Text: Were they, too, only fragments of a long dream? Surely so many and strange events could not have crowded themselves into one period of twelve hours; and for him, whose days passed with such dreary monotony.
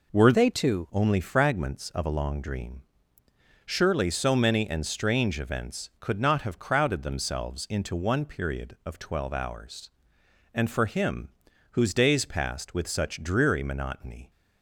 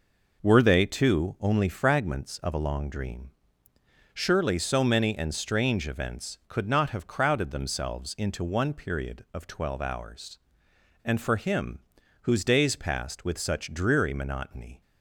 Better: second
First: changes voice from "they" to "too"; from 0.3 to 0.8 s; 0.5 s long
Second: none

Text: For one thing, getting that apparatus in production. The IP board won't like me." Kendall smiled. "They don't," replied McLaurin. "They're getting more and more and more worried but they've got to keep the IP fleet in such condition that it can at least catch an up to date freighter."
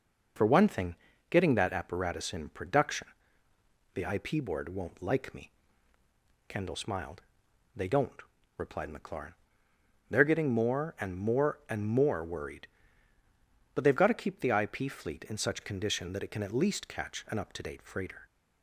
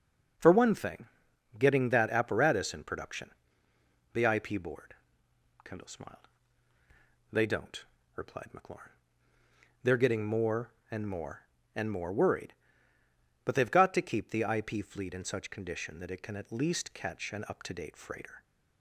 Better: first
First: none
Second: skips "won't like me"; at 5.2 s

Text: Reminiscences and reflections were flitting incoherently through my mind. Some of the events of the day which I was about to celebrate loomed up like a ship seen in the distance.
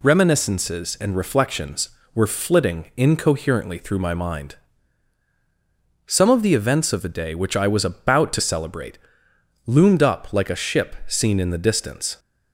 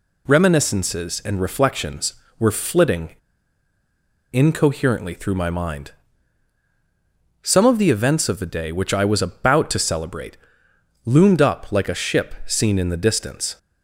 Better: first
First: pauses between "celebrate" and "loomed"; noticeable; at 8.9 s; 0.70 s long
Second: pauses between "flitting" and "incoherently"; at 3.1 s; 1.2 s long // pauses between "celebrate" and "loomed"; noticeable; at 10.3 s; 0.70 s long

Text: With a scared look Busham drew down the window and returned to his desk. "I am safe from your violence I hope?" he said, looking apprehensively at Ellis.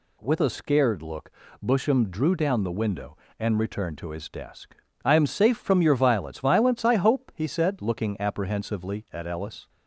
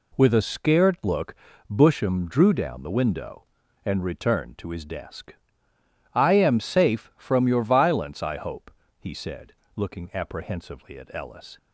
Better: second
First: pauses between "look" and "Busham"; slight; at 1.3 s; 0.34 s long // says "violence" twice; at 6.4 s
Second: pauses between "look" and "Busham"; at 1.3 s; 0.38 s long

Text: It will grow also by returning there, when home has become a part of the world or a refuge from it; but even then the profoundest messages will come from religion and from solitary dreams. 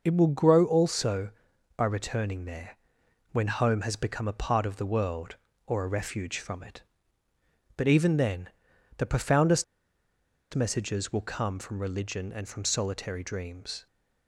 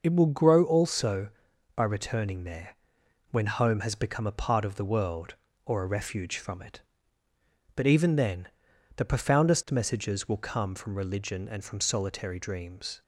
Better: second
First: pauses between "then" and "the"; noticeable; at 8.4 s; 0.48 s long // pauses between "profoundest" and "messages"; noticeable; at 9.6 s; 0.89 s long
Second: pauses between "then" and "the"; noticeable; at 8.4 s; 0.48 s long

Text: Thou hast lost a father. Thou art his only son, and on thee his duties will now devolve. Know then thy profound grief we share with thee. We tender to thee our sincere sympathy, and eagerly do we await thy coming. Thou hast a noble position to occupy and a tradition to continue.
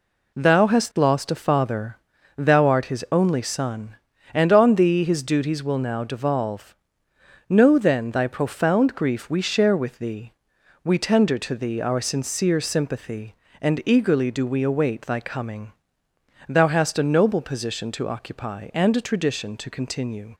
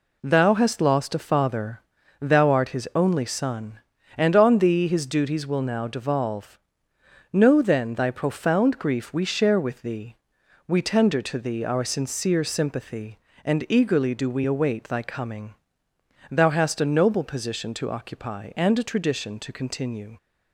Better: neither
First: none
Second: none

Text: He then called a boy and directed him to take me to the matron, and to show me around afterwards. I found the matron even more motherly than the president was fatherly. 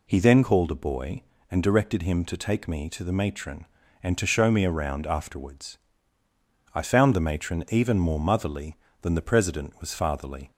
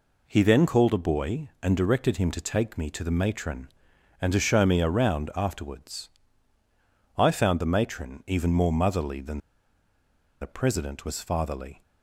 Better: first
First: none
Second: pauses between "than" and "the"; at 9.3 s; 1.0 s long

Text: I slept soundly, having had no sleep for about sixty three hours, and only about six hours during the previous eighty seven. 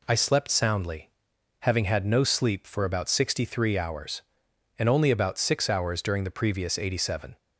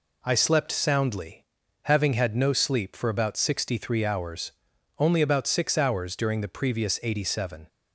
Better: first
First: none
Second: skips "and"; at 4.7 s

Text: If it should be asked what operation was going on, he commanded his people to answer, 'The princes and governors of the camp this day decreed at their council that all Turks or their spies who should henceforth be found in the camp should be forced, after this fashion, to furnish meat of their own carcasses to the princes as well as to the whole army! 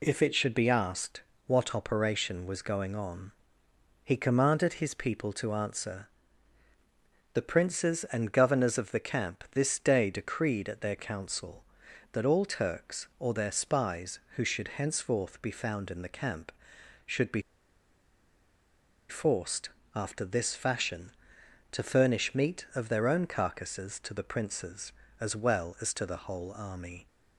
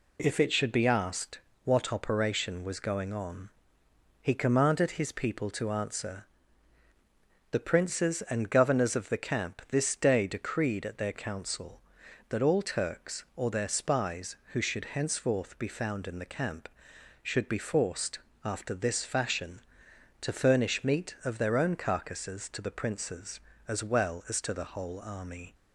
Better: second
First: pauses between "asked" and "what"; slight; at 1.2 s; 0.26 s long // pauses between "be" and "forced"; strong; at 17.4 s; 1.6 s long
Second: pauses between "asked" and "what"; slight; at 1.3 s; 0.26 s long

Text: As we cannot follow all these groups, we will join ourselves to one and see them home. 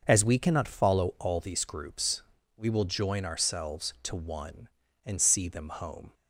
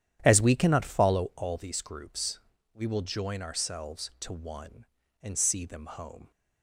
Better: first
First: none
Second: starts louder than the rest; strong; until 1.3 s; 10.5 dB

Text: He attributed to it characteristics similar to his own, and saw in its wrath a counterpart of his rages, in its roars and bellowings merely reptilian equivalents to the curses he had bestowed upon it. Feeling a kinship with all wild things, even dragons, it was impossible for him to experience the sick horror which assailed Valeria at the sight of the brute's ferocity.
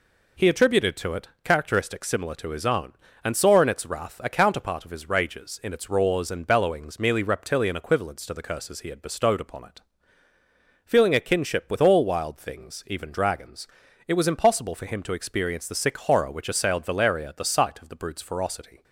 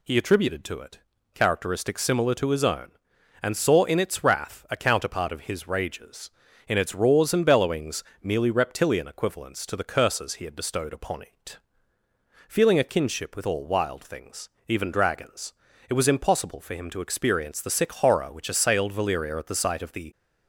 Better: first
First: none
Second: pauses between "it" and "characteristics"; slight; at 0.9 s; 0.34 s long // pauses between "bellowings" and "merely"; slight; at 8.0 s; 0.20 s long // stops before "brute's ferocity"; at 20.1 s

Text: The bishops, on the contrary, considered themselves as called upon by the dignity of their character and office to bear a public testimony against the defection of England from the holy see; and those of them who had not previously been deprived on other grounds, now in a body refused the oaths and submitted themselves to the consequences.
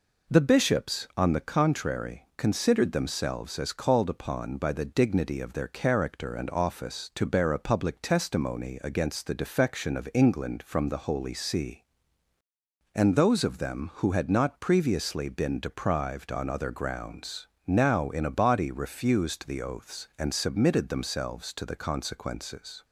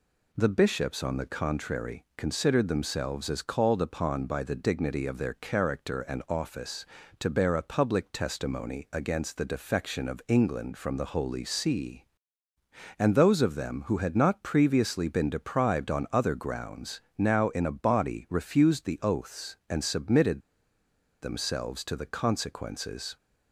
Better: first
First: none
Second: pauses between "submitted" and "themselves"; noticeable; at 20.3 s; 0.82 s long

